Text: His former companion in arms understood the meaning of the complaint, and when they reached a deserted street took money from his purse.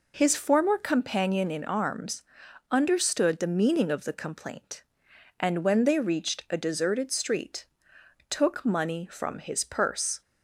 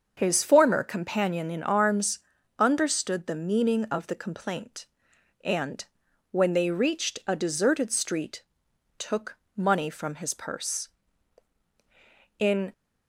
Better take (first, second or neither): first